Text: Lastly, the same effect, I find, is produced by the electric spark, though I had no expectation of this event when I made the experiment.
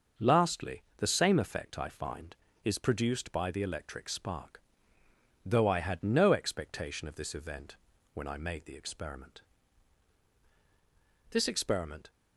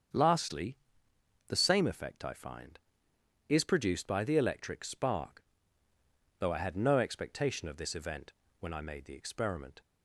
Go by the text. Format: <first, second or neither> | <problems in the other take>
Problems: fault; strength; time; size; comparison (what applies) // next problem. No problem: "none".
second | starts louder than the rest; until 1.3 s; 6.5 dB; strong in the second // pauses between "event" and "when"; at 7.7 s; 0.38 s long; slight in the second // goes on to say "This experiment"; noticeable; from 11.3 s on; 0.78 s long